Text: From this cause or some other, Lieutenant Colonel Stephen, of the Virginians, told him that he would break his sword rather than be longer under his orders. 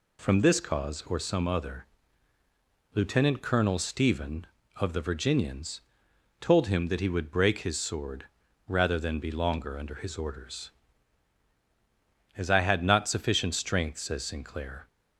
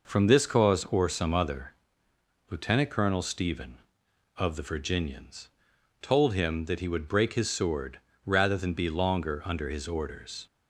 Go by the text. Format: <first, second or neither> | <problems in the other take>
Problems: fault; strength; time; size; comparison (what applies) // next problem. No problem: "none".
second | pauses between "sword" and "rather"; at 8.2 s; 0.42 s long; slight in the second // goes on to say "As I had not sufficient strength says Sinclair"; strong; from 12.3 s on; 2.5 s long